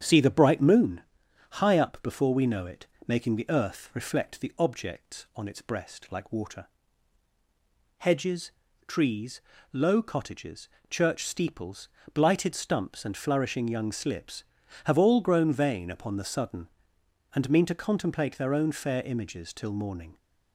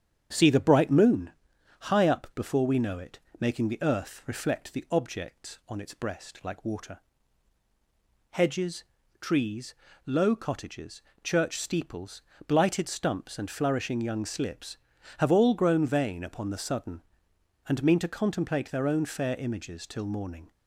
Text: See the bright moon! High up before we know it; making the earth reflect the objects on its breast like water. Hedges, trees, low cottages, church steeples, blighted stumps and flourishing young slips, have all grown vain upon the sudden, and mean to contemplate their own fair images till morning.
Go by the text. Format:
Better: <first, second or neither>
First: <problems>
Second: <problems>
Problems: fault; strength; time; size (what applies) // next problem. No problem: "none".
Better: neither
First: starts louder than the rest; strong; until 1.0 s; 8 dB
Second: starts louder than the rest; strong; until 1.3 s; 8 dB